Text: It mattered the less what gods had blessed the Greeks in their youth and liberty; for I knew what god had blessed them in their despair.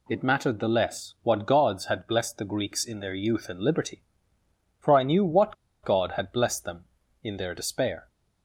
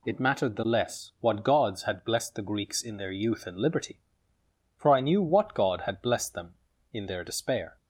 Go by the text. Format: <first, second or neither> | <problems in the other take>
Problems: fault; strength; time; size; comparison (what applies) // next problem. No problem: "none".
second | pauses between "what" and "god"; slight; at 5.5 s; 0.28 s long